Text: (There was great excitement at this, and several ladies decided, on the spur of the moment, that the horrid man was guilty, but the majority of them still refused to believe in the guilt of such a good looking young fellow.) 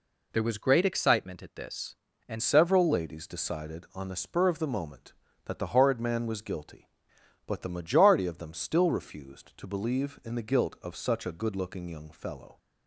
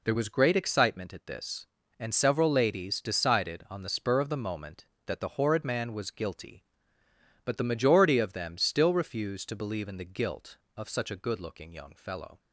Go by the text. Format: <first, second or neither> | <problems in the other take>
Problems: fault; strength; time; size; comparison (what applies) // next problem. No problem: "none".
second | changes voice at "several"; from 2.4 s on; 10.1 s long